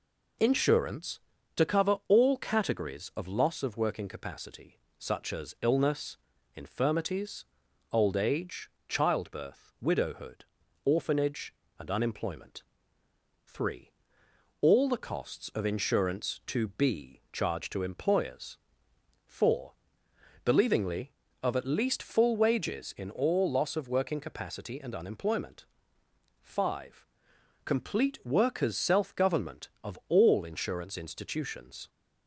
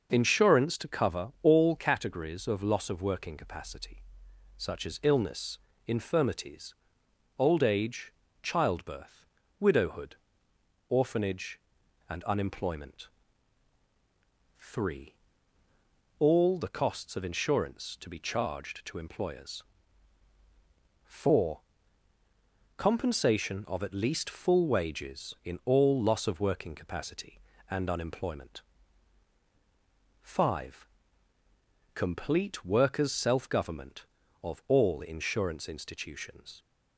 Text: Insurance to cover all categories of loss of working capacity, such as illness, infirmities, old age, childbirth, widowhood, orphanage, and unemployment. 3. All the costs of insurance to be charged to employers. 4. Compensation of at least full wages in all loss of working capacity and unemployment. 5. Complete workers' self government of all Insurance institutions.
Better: second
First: says "Believingly" for "Compensation"; at 20.4 s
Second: none

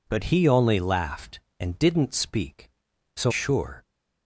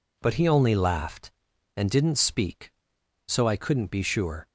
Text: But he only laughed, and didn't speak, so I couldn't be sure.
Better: second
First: skips "I couldn't be"; at 3.3 s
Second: none

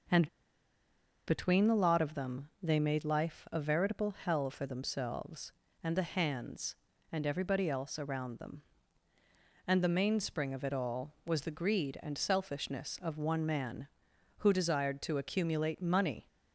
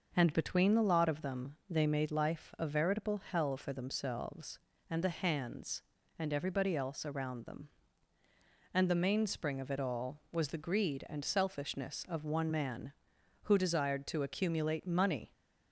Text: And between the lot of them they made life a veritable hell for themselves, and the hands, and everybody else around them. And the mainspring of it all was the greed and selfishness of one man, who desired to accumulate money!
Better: second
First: pauses between "And" and "between"; at 0.2 s; 0.99 s long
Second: none

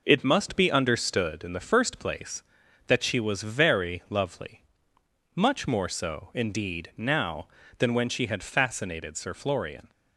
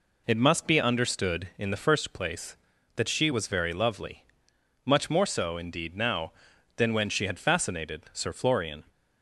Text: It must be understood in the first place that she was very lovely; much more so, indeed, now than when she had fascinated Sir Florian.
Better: neither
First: none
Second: none

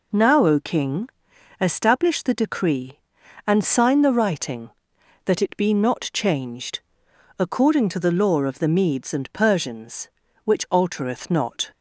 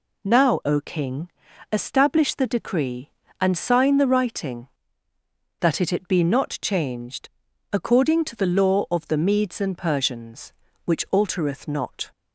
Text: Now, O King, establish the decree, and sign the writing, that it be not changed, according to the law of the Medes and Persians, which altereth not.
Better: first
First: none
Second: says "it" twice; at 5.9 s

